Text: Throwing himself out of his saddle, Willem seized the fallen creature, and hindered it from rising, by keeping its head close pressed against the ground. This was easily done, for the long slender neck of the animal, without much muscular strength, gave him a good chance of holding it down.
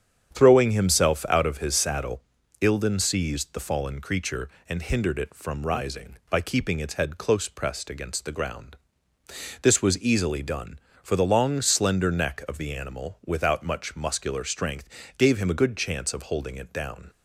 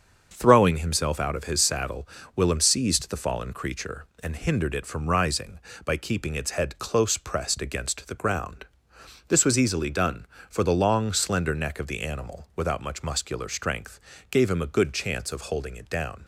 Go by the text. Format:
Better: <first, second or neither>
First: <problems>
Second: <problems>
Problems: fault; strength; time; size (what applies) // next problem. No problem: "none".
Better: second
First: starts louder than the rest; strong; until 1.3 s; 8.5 dB // says "Ilden" for "Willem"; at 2.6 s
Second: starts louder than the rest; until 1.3 s; 6.5 dB